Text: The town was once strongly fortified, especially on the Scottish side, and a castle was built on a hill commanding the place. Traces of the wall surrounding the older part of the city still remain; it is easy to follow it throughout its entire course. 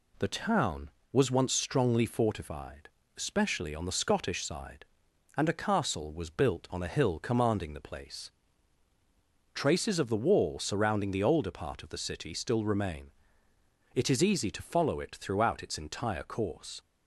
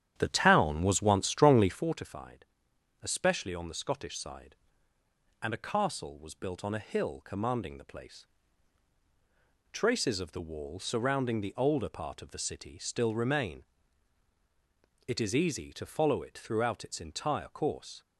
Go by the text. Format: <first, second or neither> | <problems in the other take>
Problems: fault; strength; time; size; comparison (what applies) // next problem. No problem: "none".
first | starts louder than the rest; strong; until 2.0 s; 10 dB